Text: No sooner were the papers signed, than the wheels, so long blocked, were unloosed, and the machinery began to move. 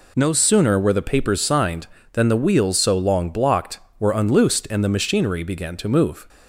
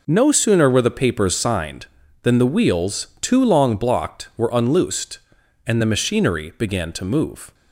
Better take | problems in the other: first | says "too" for "so"; at 3.2 s

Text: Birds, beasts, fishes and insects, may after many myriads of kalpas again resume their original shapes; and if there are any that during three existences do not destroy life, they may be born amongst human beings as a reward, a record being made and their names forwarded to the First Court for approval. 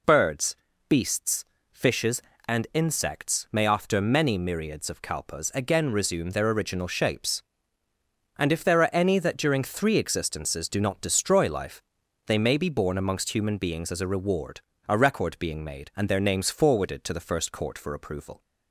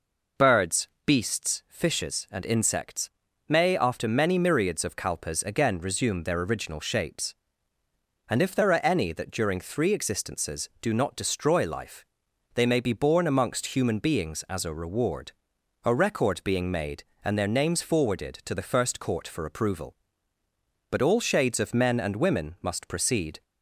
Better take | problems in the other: first | goes on to say "But all shades of men and women must proceed"; strong; from 20.8 s on; 2.5 s long

